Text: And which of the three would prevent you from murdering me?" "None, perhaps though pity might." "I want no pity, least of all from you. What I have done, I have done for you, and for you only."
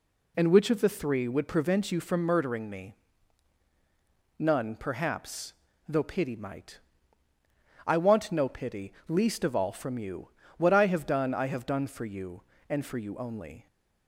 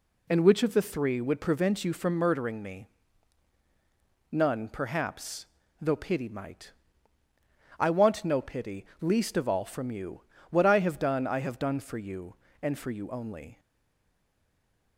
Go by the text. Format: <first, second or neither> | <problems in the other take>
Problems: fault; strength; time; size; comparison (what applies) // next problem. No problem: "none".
first | pauses between "perhaps" and "though"; slight; at 5.4 s; 0.34 s long; slight in the first // stays silent after the last word; noticeable; from 13.5 s on; 1.4 s long